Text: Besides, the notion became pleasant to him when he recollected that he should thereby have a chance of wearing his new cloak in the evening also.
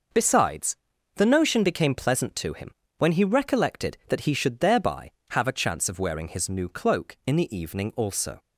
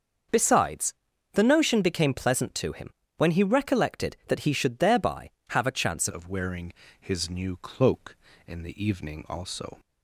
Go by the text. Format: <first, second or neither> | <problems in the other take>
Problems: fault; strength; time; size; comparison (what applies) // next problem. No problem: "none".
first | starts louder than the rest; until 1.7 s; 6.5 dB // pauses between "him" and "when"; slight; at 2.9 s; 0.26 s long; slight in the first // changes voice at "of"; from 6.1 s on; 3.6 s long // pauses between "wearing" and "his"; slight; at 6.7 s; 0.28 s long